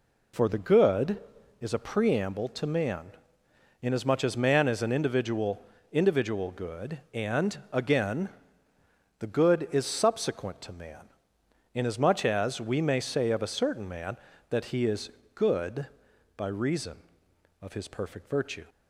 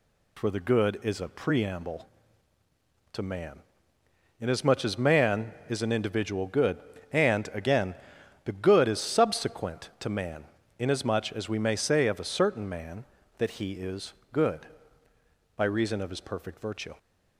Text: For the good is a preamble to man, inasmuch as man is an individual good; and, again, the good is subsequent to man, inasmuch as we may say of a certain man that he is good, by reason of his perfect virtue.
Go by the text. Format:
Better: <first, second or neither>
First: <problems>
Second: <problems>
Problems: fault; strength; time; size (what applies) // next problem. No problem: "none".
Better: second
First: says "individual" twice; at 5.9 s // pauses between "is" and "good"; slight; at 15.1 s; 0.24 s long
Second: pauses between "is" and "good"; slight; at 14.1 s; 0.22 s long